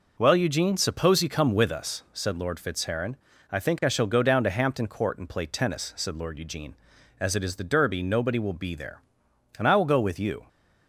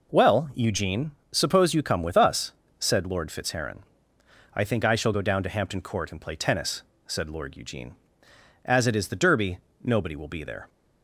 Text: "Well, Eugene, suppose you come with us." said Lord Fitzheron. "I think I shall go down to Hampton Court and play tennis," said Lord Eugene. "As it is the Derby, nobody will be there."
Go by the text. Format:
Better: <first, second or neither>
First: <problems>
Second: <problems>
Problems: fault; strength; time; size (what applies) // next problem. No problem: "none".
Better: second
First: goes on to say "And I will go with you"; noticeable; from 9.5 s on; 0.88 s long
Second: none